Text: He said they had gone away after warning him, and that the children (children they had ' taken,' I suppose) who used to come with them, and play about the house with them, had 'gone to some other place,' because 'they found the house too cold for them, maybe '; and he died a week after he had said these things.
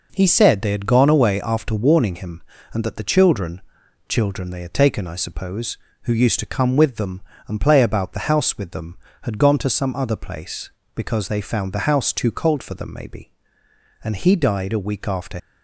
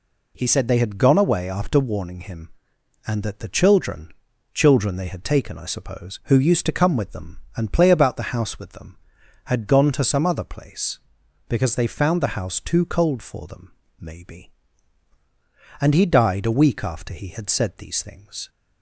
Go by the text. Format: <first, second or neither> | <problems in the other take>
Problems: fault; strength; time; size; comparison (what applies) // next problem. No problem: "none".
second | stops before "he had said these things"; at 15.3 s